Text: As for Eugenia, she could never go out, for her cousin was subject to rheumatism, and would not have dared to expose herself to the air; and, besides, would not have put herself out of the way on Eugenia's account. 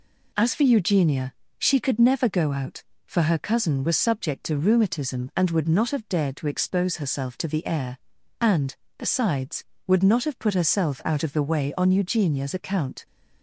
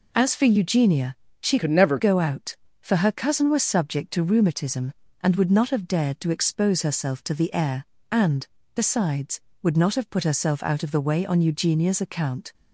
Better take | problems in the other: first | changes voice from "could" to "never"; from 1.5 to 1.9 s; 0.4 s long

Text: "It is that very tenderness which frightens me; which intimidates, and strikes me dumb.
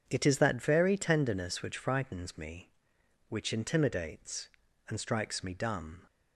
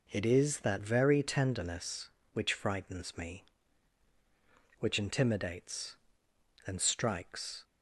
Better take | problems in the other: first | stops before "me dumb"; at 7.6 s

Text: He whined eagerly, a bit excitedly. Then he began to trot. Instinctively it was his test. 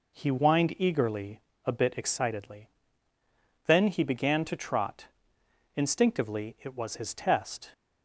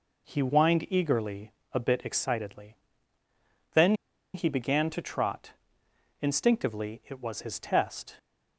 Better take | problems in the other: first | pauses between "Then" and "he"; at 3.9 s; 0.40 s long

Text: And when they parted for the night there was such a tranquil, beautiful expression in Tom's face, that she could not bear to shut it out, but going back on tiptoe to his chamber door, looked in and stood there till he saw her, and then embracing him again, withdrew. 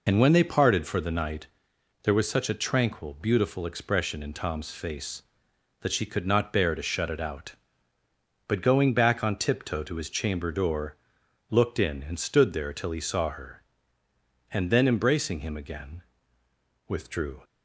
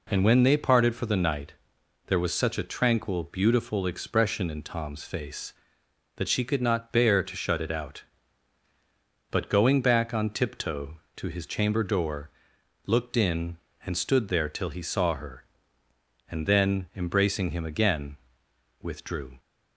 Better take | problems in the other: second | loses the start of "And"; at 0.0 s; 40 ms // pauses between "night" and "there"; noticeable; at 1.4 s; 0.56 s long; noticeable in the second

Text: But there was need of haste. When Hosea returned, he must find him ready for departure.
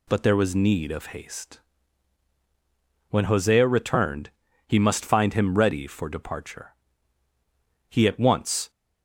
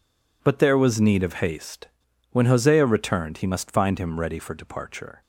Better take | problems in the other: second | goes on to say "He at once"; noticeable; from 7.8 s on; 0.80 s long

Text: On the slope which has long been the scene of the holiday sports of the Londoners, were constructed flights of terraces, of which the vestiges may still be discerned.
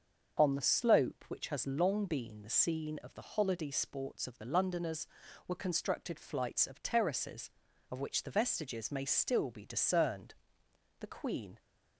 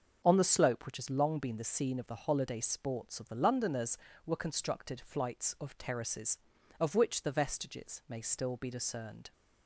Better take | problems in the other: second | starts louder than the rest; until 1.4 s; 6.5 dB; also in the second // goes on to say "The Queen"; from 11.0 s on; 0.58 s long

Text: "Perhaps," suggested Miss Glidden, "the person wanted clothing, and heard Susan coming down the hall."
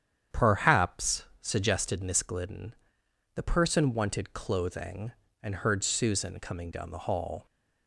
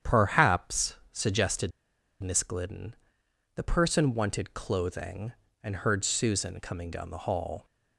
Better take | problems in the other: first | starts louder than the rest; strong; until 1.2 s; 9 dB; strong in the first // pauses between "suggested" and "Miss"; noticeable; at 1.7 s; 0.51 s long

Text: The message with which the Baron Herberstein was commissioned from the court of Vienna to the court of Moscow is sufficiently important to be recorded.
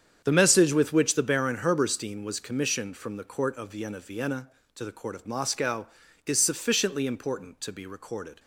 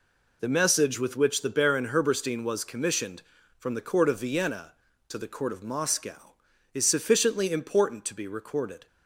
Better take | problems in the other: second | starts louder than the rest; strong; until 1.2 s; 8 dB // says "Vienna" twice; at 3.9 s

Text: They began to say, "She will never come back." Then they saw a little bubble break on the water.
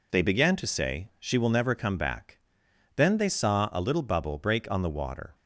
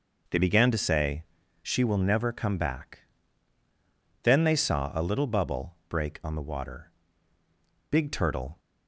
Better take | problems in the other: first | goes on to say "Big Turtle"; noticeable; from 7.9 s on; 0.68 s long

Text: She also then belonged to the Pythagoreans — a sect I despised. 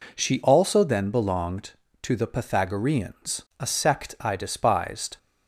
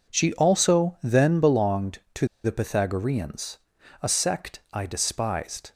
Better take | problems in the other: first | pauses between "to" and "the"; slight; at 2.2 s; 0.18 s long

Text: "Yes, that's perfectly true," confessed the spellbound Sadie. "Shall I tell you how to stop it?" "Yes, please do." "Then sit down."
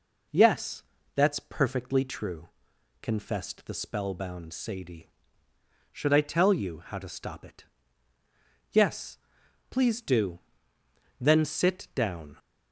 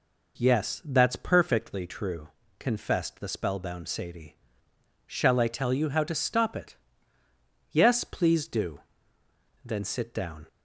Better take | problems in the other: second | says "Should" for "Shall"; at 5.9 s

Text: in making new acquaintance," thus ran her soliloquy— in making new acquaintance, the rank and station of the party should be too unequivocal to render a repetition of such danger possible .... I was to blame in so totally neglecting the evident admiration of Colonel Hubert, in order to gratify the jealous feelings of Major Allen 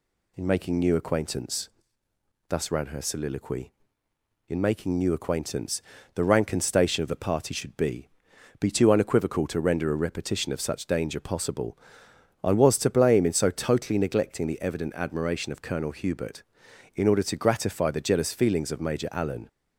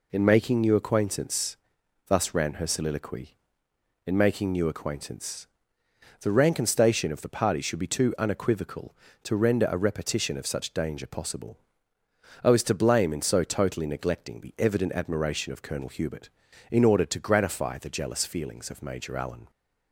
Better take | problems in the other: second | says "be" twice; at 8.5 s

